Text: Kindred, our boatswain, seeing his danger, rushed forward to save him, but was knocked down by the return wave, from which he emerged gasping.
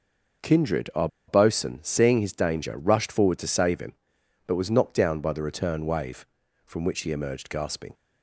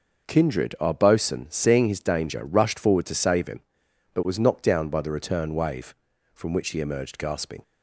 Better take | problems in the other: second | starts louder than the rest; noticeable; until 1.6 s; 6 dB; noticeable in the second // pauses between "our" and "boatswain"; slight; at 1.0 s; 0.20 s long

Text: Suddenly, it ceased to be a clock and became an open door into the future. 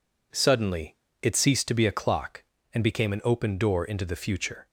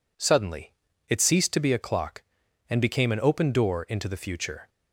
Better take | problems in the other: neither | none

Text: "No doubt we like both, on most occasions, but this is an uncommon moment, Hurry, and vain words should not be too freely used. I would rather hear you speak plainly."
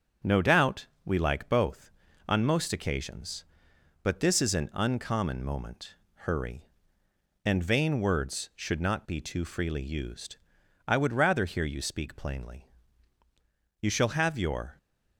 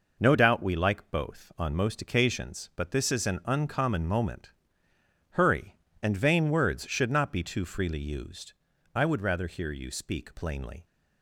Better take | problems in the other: second | starts louder than the rest; strong; until 1.4 s; 7 dB // pauses between "doubt" and "we"; slight; at 0.8 s; 0.18 s long // goes on to say "You shall have your"; noticeable; from 13.8 s on; 0.96 s long

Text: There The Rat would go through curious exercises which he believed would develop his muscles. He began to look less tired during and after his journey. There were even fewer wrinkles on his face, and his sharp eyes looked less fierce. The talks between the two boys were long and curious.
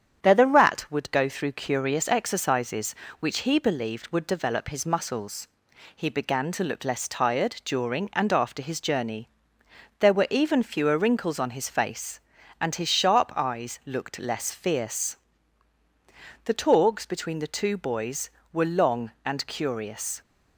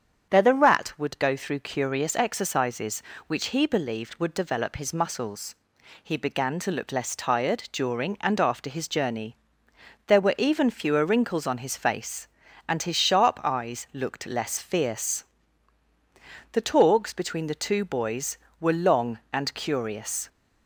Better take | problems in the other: second | gets quieter; slight; throughout; 2 dB // starts louder than the rest; strong; until 1.2 s; 8.5 dB; strong in the second

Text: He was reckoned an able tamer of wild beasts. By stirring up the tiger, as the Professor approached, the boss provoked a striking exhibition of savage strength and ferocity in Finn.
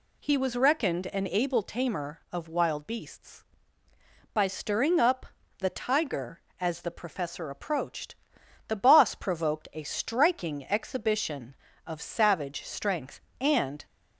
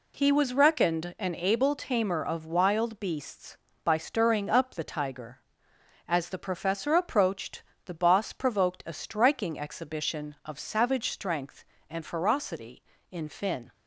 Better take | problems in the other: second | pauses between "up" and "the"; slight; at 5.2 s; 0.34 s long // stops before "ferocity in Finn"; at 13.8 s

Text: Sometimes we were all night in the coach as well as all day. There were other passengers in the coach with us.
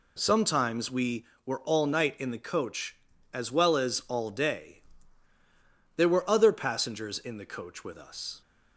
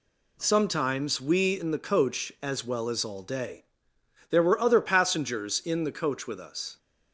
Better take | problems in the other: first | skips "were all night"; at 1.5 s

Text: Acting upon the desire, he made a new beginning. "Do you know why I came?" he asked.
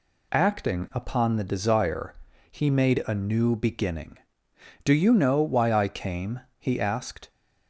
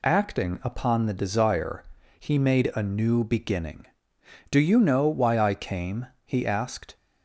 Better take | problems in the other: neither | none

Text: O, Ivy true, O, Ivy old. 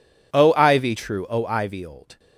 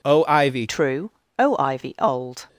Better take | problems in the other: first | changes voice at "true"; from 0.6 s on; 1.8 s long

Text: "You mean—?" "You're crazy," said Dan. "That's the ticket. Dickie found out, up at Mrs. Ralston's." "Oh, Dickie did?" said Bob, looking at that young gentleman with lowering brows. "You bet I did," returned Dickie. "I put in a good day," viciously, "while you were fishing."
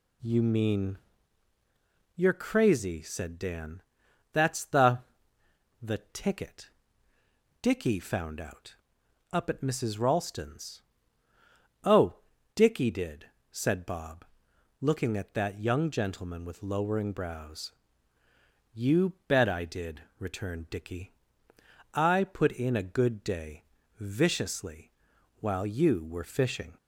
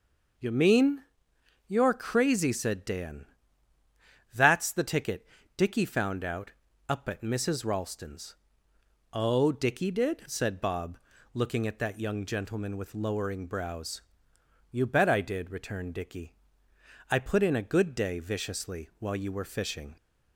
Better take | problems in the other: second | says "the" twice; at 5.8 s

